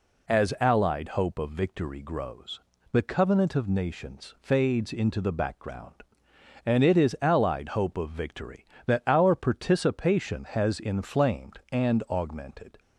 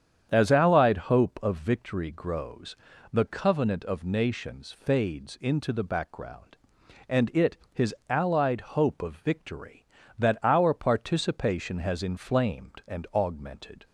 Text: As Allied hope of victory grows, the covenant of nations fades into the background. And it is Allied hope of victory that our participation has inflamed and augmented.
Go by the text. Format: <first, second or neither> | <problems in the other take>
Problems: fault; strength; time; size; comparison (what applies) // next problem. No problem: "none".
first | starts louder than the rest; strong; until 1.4 s; 8.5 dB // says "his" for "is"; at 7.7 s